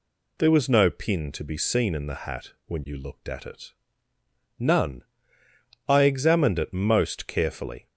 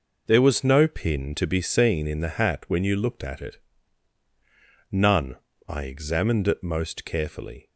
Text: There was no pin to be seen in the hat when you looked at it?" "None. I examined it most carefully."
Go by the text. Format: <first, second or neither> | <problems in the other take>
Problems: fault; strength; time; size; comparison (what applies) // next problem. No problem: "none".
neither | none